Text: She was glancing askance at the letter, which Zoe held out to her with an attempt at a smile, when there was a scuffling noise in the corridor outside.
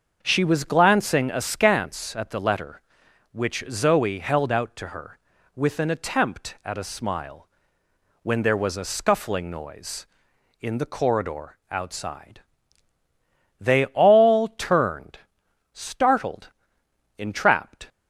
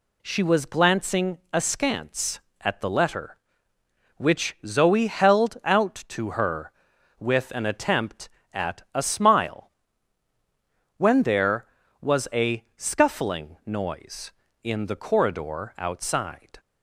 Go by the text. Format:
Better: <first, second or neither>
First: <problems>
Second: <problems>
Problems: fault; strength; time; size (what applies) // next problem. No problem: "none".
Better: second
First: starts louder than the rest; until 1.2 s; 6.5 dB // goes on to say "They all turned startled ENTRAPPED"; strong; from 13.6 s on; 4.2 s long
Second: none